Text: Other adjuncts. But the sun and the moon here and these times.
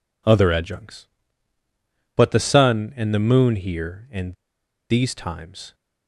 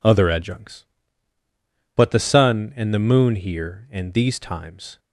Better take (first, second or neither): second